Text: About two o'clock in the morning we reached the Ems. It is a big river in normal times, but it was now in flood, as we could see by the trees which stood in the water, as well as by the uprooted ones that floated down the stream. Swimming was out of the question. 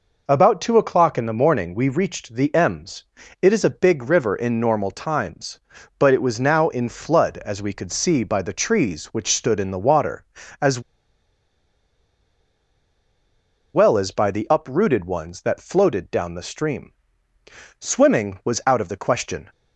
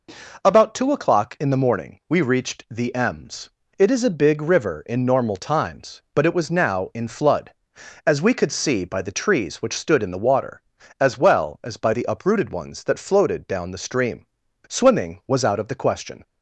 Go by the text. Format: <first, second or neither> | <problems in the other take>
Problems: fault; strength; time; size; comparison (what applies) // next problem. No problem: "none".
second | pauses between "as" and "well"; strong; at 10.7 s; 2.9 s long